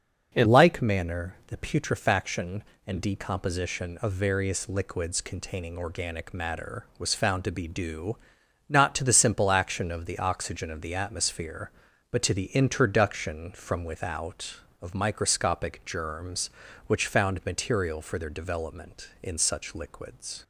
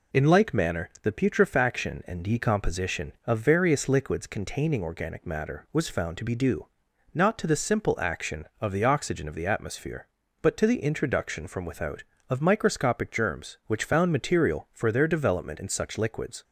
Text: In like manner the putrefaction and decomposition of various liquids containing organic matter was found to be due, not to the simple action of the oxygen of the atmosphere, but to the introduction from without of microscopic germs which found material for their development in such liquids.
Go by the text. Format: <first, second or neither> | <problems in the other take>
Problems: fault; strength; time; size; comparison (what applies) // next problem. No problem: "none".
second | starts louder than the rest; until 1.3 s; 6.5 dB // changes voice at "like"; from 0.4 s on; 20.0 s long